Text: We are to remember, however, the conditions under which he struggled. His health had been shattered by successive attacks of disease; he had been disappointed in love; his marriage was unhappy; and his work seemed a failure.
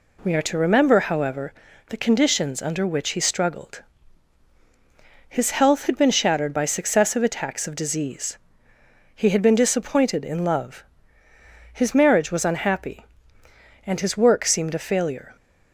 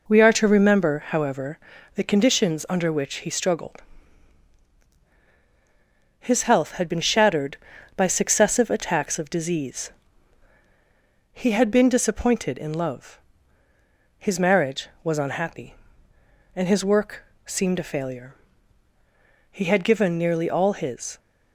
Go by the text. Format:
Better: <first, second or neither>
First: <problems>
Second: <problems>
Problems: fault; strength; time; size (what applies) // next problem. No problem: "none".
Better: first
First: none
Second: pauses between "work" and "seemed"; slight; at 17.2 s; 0.20 s long // goes on to say "He had given nearly all his"; strong; from 19.5 s on; 1.6 s long